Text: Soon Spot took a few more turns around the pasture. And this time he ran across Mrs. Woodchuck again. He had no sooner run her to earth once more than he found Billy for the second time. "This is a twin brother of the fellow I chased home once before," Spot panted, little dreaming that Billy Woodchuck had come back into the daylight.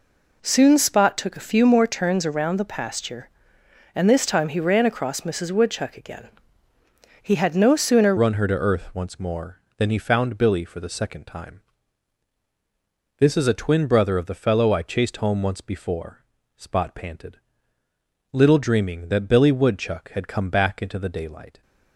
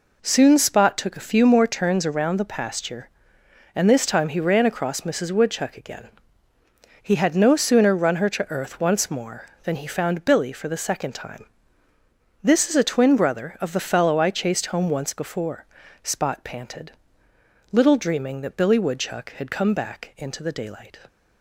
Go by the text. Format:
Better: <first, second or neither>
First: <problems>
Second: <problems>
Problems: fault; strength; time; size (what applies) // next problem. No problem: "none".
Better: second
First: changes voice at "run"; from 8.1 s on; 13.5 s long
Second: none